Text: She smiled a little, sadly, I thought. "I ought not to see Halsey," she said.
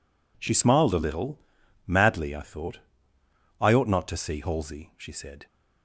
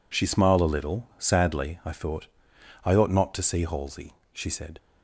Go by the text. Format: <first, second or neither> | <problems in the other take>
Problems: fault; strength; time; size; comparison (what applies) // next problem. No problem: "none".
second | says "madly" for "sadly"; at 1.8 s